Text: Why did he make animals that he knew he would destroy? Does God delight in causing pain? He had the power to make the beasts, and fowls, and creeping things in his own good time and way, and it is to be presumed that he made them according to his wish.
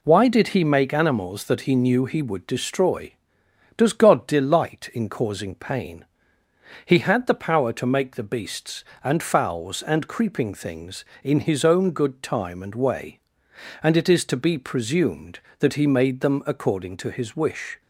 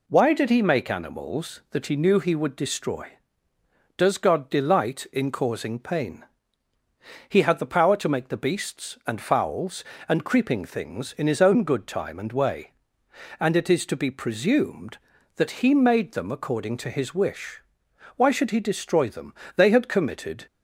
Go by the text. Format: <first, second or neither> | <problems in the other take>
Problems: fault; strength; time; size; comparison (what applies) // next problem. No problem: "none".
first | goes on to say "Why should he destroy them They had committed"; strong; from 18.1 s on; 2.3 s long